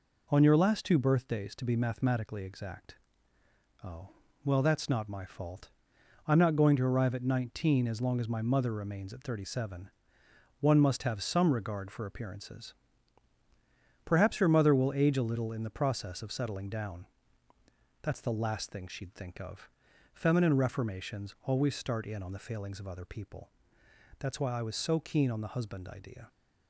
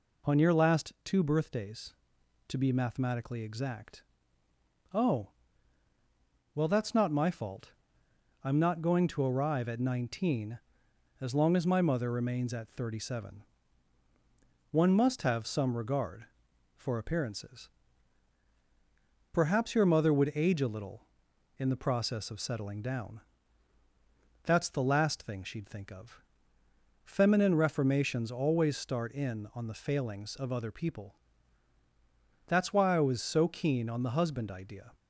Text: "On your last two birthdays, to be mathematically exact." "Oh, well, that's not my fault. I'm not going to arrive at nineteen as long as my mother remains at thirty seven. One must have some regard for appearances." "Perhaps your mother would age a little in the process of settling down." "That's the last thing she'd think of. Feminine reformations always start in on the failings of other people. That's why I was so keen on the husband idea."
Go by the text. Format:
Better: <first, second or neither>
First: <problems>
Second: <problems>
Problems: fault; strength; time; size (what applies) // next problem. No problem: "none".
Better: second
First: says "will" for "would"; at 14.7 s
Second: none